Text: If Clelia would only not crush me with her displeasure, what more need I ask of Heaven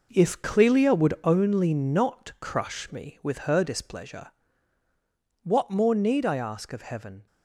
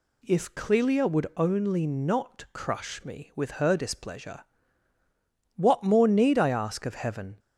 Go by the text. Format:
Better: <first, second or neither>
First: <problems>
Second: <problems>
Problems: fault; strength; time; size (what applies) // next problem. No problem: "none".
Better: second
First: gets quieter; strong; throughout; 9.5 dB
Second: none